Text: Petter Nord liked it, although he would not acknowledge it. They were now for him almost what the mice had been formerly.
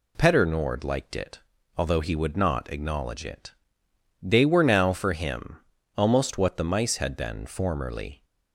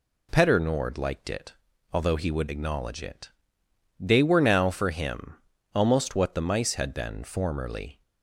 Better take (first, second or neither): first